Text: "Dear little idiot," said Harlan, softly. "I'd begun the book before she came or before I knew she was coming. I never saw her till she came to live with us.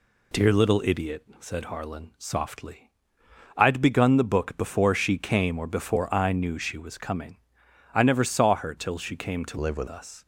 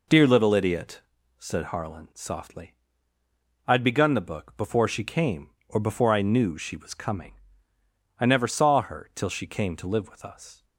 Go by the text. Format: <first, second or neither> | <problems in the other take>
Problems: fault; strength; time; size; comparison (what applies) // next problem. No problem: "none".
second | changes voice from "live" to "with"; from 9.5 to 9.8 s; 0.3 s long